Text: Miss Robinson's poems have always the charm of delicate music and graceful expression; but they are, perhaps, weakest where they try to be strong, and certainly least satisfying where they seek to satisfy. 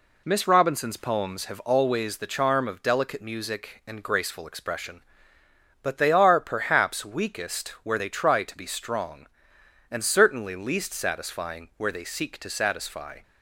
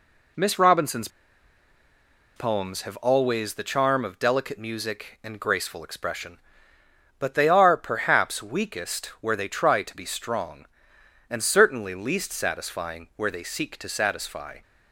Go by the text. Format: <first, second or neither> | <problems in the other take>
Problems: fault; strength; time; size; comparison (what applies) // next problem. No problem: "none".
first | pauses between "Robinson's" and "poems"; strong; at 1.0 s; 1.2 s long // pauses between "weakest" and "where"; slight; at 9.0 s; 0.16 s long; slight in the first